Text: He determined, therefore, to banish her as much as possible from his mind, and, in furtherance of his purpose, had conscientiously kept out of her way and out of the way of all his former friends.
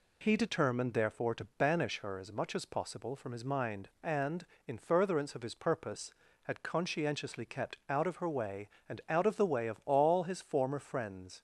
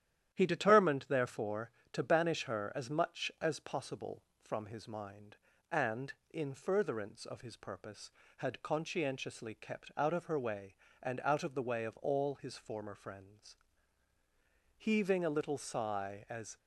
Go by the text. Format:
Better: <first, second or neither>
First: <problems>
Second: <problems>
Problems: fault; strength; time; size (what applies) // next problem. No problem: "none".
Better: first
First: none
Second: starts louder than the rest; strong; until 1.3 s; 10.5 dB // goes on to say "Heaving a little sigh as"; strong; from 14.7 s on; 1.8 s long